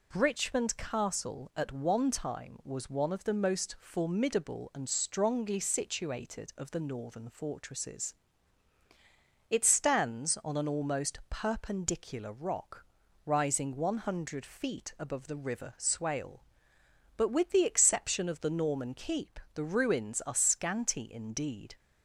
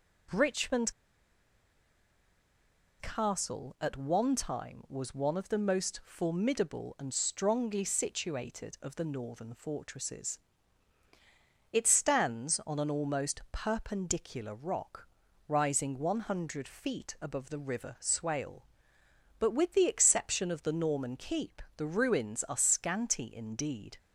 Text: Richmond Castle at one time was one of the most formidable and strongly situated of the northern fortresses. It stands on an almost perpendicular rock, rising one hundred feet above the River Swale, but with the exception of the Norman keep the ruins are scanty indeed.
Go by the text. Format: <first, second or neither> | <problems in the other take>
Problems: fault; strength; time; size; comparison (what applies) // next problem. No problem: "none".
first | pauses between "Richmond" and "Castle"; strong; at 0.9 s; 2.0 s long // pauses between "keep" and "the"; slight; at 21.6 s; 0.16 s long; slight in the first